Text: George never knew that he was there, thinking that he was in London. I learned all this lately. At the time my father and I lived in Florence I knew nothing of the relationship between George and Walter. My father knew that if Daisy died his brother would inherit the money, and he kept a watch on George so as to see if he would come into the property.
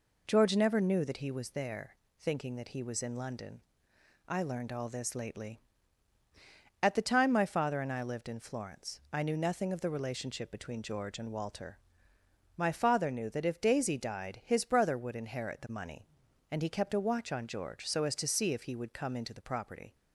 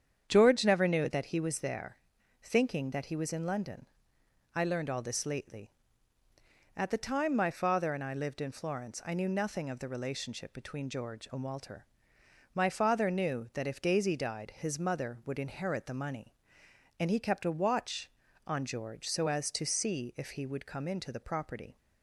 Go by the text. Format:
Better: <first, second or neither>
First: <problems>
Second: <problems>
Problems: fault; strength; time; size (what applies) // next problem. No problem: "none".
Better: first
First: none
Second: starts louder than the rest; strong; until 1.2 s; 8 dB // says "mother" for "brother"; at 14.7 s